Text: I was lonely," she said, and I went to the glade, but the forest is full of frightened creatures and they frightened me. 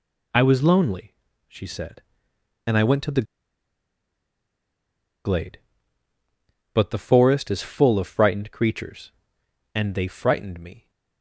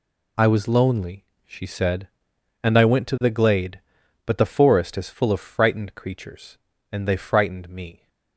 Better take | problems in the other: second | pauses between "the" and "glade"; strong; at 3.2 s; 2.0 s long

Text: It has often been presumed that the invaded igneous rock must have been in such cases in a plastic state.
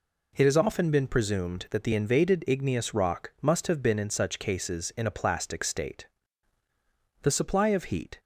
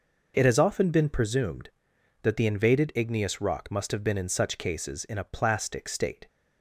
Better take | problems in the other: second | goes on to say "The supply of heat"; noticeable; from 7.2 s on; 0.98 s long

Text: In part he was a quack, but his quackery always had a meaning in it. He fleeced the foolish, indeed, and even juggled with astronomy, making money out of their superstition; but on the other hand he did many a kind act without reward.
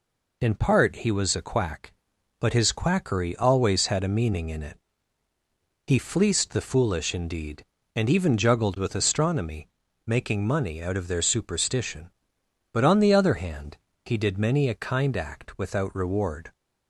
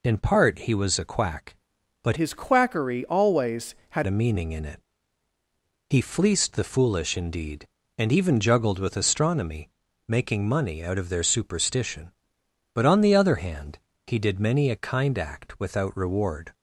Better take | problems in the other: first | changes voice from "his" to "had"; from 2.1 to 4.0 s; 1.9 s long // pauses between "hand" and "he"; slight; at 13.7 s; 0.26 s long; slight in the first

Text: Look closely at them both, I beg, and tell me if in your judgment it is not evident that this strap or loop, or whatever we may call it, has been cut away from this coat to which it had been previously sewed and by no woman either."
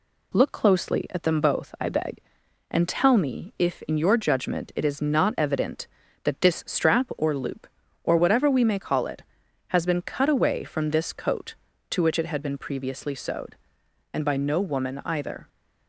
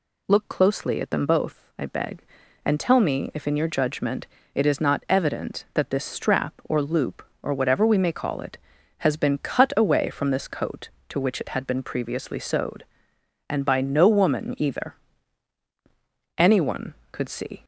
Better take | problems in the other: first | pauses between "judgment" and "it"; slight; at 4.2 s; 0.28 s long // goes on to say "Anyone could see"; noticeable; from 16.3 s on; 1.2 s long

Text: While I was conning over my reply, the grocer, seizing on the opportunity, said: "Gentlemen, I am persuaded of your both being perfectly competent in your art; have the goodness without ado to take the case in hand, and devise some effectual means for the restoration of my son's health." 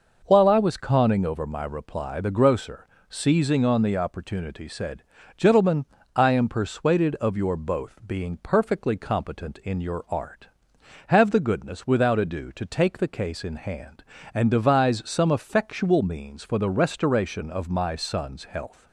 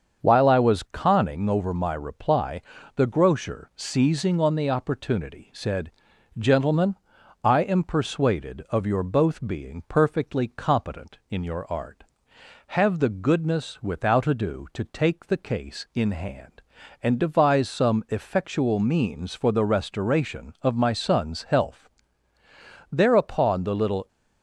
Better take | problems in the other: first | starts louder than the rest; until 1.2 s; 7 dB // goes on to say "Thereupon the little"; noticeable; from 22.9 s on; 1.1 s long

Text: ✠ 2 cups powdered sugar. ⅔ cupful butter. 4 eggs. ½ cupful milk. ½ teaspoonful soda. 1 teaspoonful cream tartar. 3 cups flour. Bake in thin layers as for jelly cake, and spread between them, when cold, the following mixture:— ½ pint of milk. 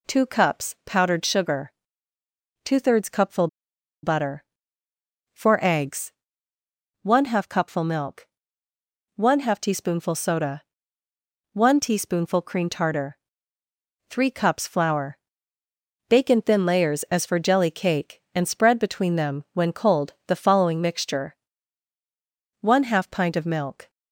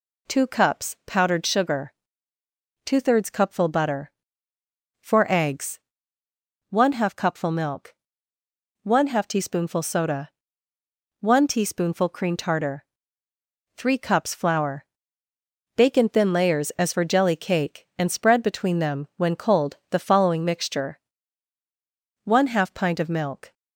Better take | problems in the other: second | pauses between "cupful" and "butter"; noticeable; at 3.4 s; 0.56 s long

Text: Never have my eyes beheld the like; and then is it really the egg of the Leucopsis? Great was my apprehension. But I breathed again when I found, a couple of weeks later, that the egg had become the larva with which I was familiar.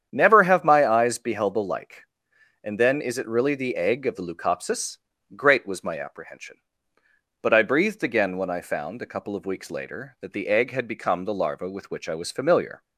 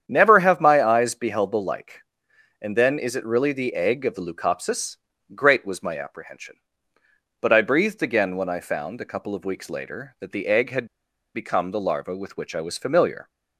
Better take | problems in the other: first | starts louder than the rest; strong; until 1.0 s; 8.5 dB; strong in the first // pauses between "had" and "become"; noticeable; at 10.8 s; 0.48 s long

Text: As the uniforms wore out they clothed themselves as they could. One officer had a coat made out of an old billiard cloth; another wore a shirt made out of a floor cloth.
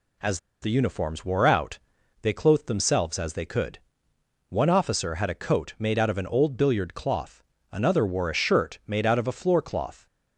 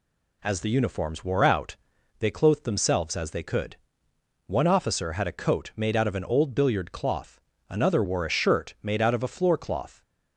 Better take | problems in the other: second | pauses between "As" and "the"; slight; at 0.3 s; 0.22 s long // pauses between "out" and "they"; at 1.7 s; 0.44 s long; also in the second

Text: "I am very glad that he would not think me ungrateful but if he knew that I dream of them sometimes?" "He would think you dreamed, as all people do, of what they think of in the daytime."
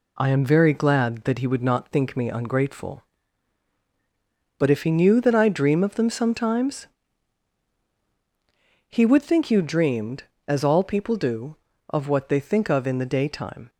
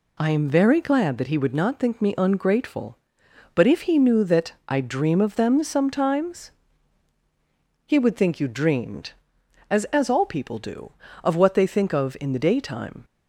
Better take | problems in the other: first | says "as" twice; at 9.9 s

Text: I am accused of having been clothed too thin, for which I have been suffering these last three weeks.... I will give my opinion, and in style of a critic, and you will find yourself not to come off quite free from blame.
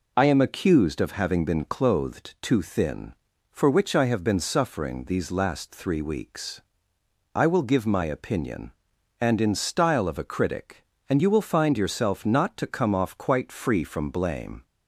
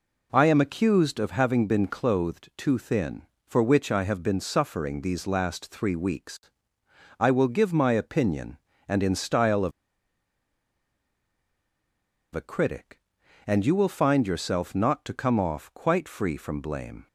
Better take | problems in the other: first | pauses between "of" and "a"; strong; at 9.7 s; 2.6 s long

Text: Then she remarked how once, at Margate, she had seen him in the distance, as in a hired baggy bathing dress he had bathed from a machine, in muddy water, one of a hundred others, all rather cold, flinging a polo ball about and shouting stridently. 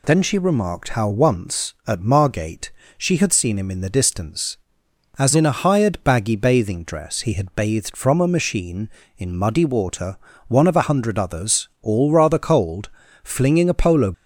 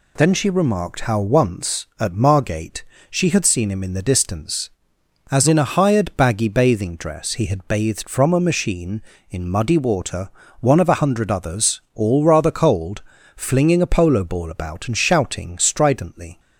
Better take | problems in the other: second | stops before "ball about and shouting stridently"; at 14.1 s

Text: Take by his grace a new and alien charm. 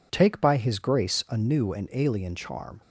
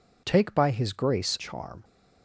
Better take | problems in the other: first | skips "a new and alien"; at 1.3 s

